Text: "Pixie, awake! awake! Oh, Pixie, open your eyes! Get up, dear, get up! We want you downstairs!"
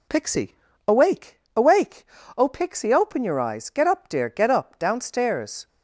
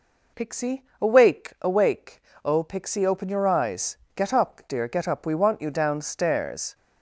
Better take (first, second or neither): second